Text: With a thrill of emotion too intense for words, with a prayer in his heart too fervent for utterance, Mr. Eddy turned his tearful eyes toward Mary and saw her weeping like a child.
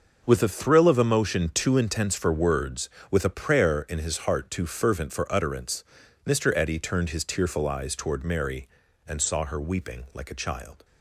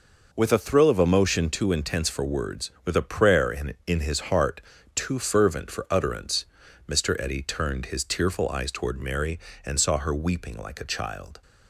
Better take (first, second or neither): first